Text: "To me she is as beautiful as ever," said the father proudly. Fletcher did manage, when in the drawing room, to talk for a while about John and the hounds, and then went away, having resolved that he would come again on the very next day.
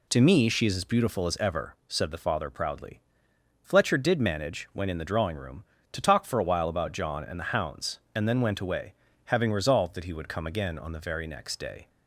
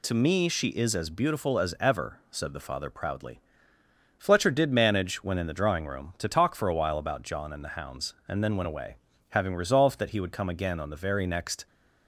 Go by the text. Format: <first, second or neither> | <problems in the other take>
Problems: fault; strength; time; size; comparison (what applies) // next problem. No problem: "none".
first | stops before "day"; at 11.6 s